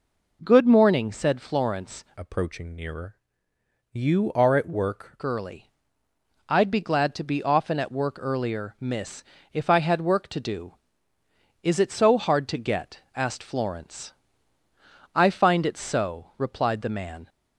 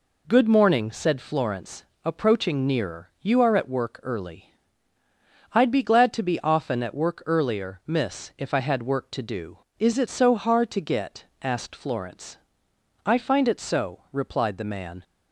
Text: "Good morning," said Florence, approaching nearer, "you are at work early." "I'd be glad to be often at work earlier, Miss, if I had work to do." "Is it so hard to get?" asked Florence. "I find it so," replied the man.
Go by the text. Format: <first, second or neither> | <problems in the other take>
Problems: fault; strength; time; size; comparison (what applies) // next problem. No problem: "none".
second | changes voice from "approaching" to "work"; from 2.1 to 5.1 s; 3.0 s long